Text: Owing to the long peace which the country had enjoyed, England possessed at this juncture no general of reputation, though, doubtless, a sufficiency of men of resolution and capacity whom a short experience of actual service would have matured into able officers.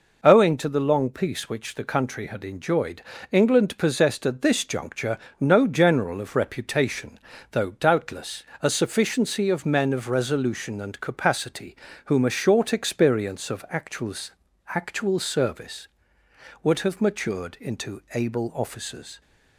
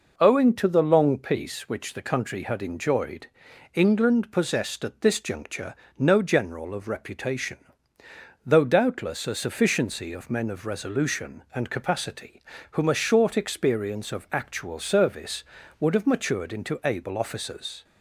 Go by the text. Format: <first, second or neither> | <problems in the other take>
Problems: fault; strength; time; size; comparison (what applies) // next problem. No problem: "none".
second | pauses between "juncture" and "no"; slight; at 5.1 s; 0.22 s long; slight in the second // pauses between "capacity" and "whom"; slight; at 11.7 s; 0.30 s long; slight in the second // says "actual" twice; at 14.7 s